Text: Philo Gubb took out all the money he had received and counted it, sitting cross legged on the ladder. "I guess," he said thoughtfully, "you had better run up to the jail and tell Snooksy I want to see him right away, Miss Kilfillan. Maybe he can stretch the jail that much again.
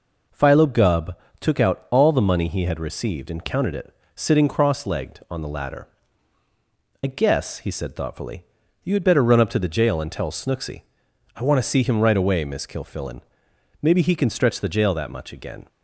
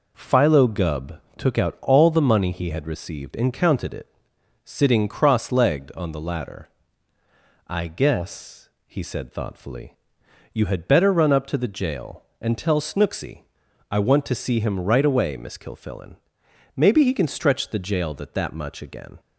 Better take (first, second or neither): first